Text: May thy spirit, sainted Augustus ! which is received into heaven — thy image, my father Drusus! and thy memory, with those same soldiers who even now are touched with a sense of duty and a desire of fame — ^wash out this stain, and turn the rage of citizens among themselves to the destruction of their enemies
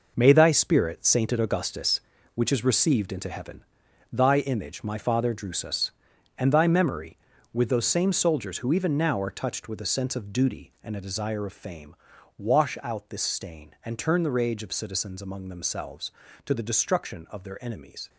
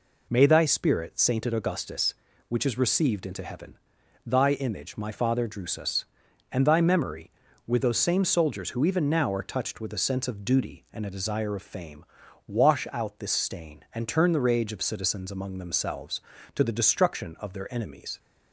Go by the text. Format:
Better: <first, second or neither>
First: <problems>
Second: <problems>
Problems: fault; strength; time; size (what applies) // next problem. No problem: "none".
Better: second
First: gets quieter; strong; throughout; 9.5 dB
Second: none